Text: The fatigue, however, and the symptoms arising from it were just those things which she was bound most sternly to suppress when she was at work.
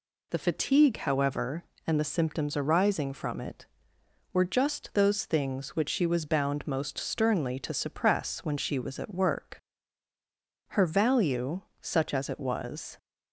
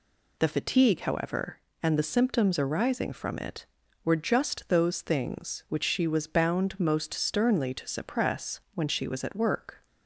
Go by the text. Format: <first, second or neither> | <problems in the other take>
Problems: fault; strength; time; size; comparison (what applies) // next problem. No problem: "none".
second | goes on to say "Her value such as it was"; strong; from 10.6 s on; 2.2 s long